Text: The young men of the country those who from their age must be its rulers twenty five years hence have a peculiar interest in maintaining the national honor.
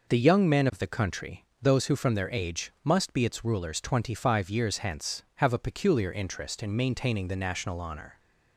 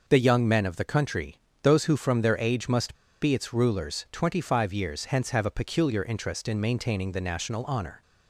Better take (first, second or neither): first